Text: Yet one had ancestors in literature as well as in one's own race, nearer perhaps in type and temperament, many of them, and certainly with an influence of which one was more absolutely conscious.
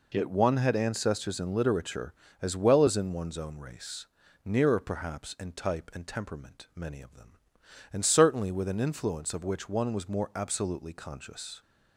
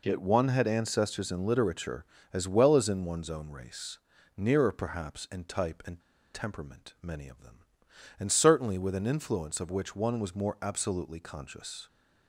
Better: first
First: none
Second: pauses between "and" and "temperament"; slight; at 5.9 s; 0.35 s long

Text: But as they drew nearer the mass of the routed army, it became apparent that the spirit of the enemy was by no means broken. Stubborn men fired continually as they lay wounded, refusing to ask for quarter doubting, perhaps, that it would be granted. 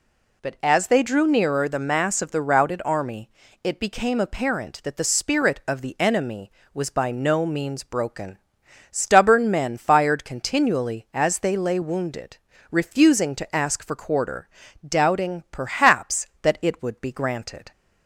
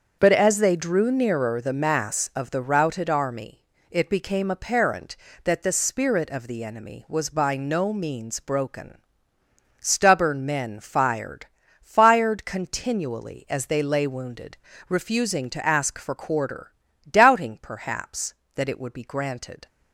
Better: first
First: pauses between "quarter" and "doubting"; at 14.4 s; 0.40 s long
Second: starts louder than the rest; until 1.2 s; 7 dB // says "fired" twice; at 11.8 s // pauses between "quarter" and "doubting"; at 16.7 s; 0.38 s long

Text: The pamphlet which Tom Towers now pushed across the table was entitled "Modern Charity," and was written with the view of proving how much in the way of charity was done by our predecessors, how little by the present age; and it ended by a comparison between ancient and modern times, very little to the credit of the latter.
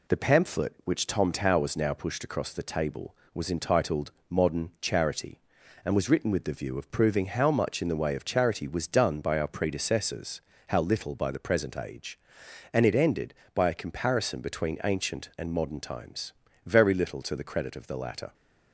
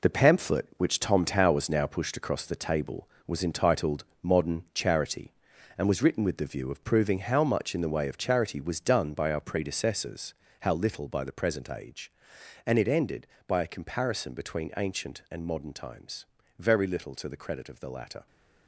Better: first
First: pauses between "entitled" and "Modern"; slight; at 4.1 s; 0.18 s long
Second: gets quieter; strong; throughout; 9 dB // pauses between "entitled" and "Modern"; slight; at 4.0 s; 0.18 s long

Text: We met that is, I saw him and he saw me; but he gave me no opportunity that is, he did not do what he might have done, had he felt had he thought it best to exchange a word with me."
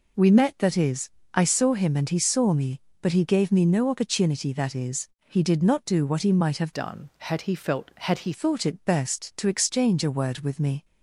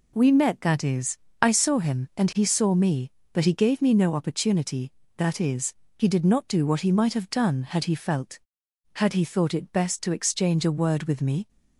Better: second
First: changes voice from "done" to "he"; from 6.7 to 8.3 s; 1.6 s long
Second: none

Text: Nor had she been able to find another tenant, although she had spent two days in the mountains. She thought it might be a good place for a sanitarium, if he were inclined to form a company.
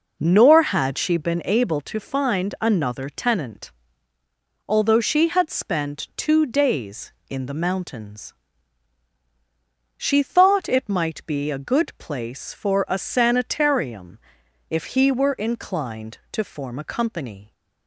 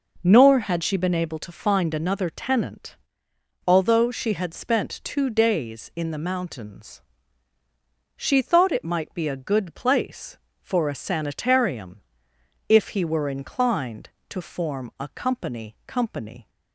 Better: first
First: none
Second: says "company" twice; at 15.8 s

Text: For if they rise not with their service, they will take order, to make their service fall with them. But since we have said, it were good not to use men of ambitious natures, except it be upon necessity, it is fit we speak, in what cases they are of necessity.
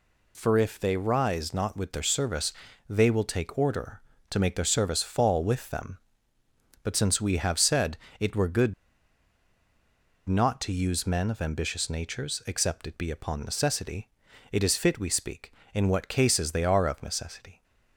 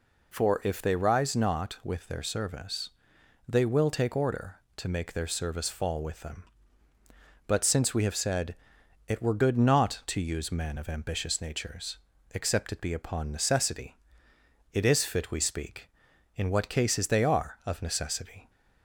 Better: second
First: pauses between "good" and "not"; strong; at 8.7 s; 1.5 s long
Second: none

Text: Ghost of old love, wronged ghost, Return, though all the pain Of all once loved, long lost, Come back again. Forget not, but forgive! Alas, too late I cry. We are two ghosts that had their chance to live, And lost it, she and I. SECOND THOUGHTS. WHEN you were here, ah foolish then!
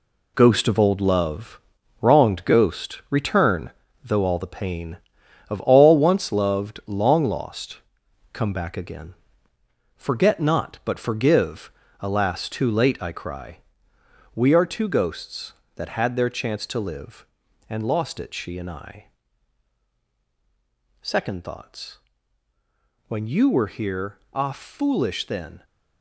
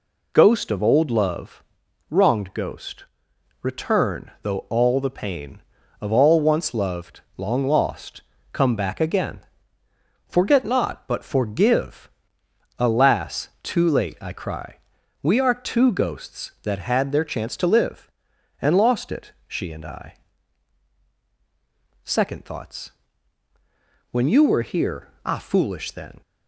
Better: second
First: gets quieter; strong; throughout; 8 dB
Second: none

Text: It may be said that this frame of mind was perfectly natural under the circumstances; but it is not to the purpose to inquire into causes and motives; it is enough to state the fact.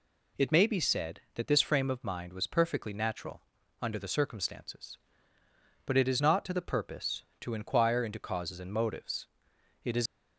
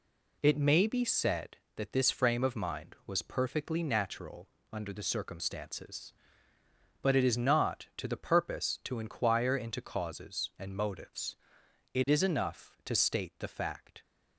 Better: second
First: pauses between "natural" and "under"; at 3.4 s; 0.40 s long // stops before "enough to state the fact"; at 10.0 s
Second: pauses between "natural" and "under"; slight; at 4.4 s; 0.22 s long

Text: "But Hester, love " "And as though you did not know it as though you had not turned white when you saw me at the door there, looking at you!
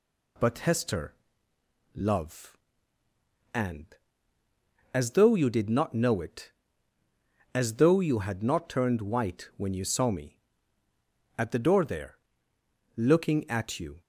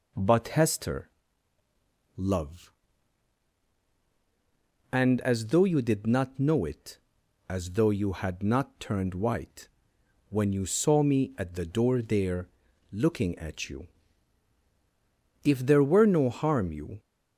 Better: first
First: none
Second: pauses between "white" and "when"; noticeable; at 9.6 s; 0.58 s long // goes on to say "If there were no harm you"; from 15.4 s on; 1.5 s long

